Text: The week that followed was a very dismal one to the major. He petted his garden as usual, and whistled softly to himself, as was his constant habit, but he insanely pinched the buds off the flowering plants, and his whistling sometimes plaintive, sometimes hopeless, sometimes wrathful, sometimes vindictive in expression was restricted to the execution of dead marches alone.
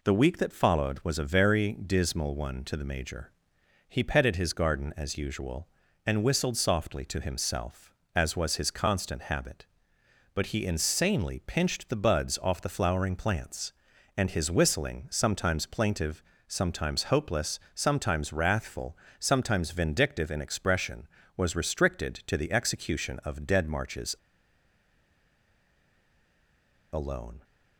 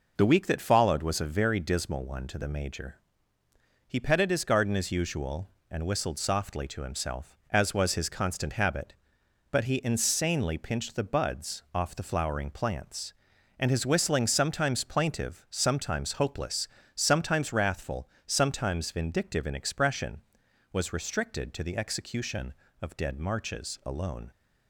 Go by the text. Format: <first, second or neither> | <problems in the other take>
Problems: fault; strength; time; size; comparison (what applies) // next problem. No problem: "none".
second | pauses between "marches" and "alone"; strong; at 24.1 s; 2.7 s long